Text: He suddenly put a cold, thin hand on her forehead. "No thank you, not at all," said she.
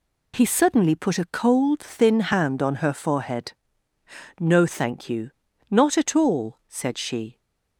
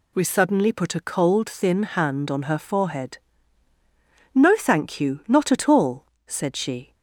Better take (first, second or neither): first